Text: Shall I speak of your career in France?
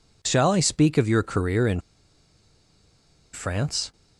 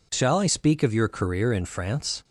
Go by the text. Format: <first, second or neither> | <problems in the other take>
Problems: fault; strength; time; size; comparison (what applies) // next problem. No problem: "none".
second | pauses between "in" and "France"; strong; at 1.7 s; 1.5 s long